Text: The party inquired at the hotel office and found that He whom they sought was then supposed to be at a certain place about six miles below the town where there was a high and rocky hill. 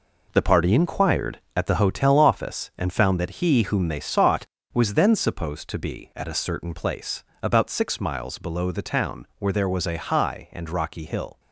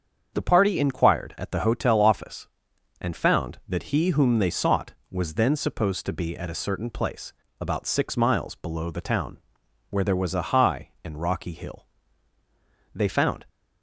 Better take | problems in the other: first | starts louder than the rest; strong; until 1.3 s; 7 dB // pauses between "place" and "about"; slight; at 7.3 s; 0.28 s long; slight in the first // pauses between "town" and "where"; noticeable; at 9.3 s; 0.52 s long // goes on to say "They found"; from 12.9 s on; 0.52 s long

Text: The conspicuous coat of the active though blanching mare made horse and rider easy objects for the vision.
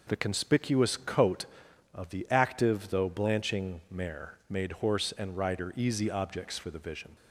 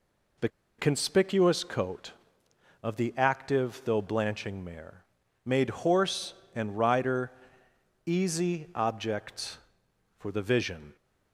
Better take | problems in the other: first | pauses between "The" and "conspicuous"; slight; at 0.4 s; 0.30 s long // pauses between "mare" and "made"; at 5.0 s; 0.40 s long // pauses between "rider" and "easy"; noticeable; at 7.2 s; 0.76 s long

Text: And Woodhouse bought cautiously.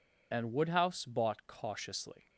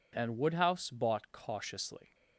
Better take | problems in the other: second | loses the start of "And"; at 0.3 s; 30 ms

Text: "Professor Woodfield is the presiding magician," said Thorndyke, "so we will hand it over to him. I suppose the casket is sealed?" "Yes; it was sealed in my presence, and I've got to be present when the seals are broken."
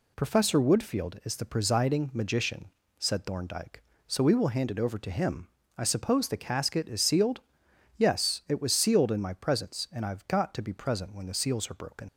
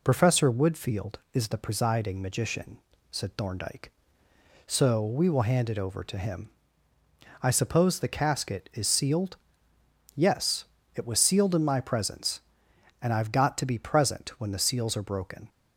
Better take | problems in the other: second | leaves "broken" unfinished; at 12.0 s; 55 ms

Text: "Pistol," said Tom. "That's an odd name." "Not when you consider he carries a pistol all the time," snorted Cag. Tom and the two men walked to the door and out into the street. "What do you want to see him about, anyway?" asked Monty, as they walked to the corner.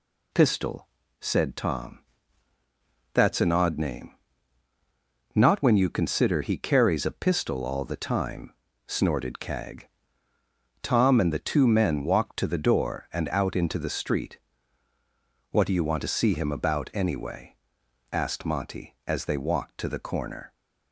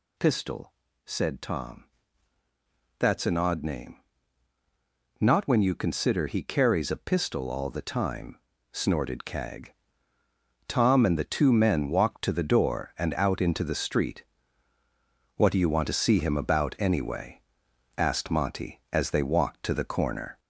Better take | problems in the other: first | gets louder; slight; throughout; 2.5 dB

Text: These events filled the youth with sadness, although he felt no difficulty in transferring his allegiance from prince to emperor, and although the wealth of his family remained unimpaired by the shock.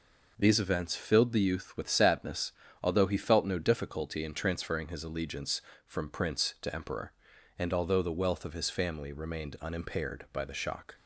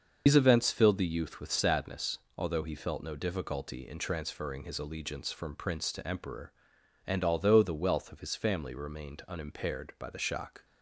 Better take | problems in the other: first | loses the start of "These"; at 0.2 s; 90 ms // starts louder than the rest; until 1.2 s; 6.5 dB

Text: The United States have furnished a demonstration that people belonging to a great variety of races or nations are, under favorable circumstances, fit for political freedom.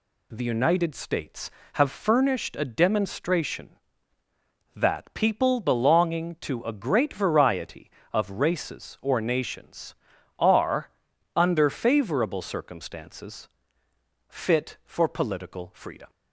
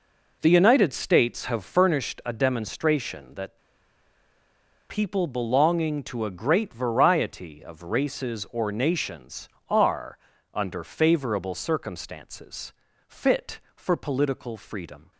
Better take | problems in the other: first | pauses between "that" and "people"; strong; at 3.5 s; 1.3 s long

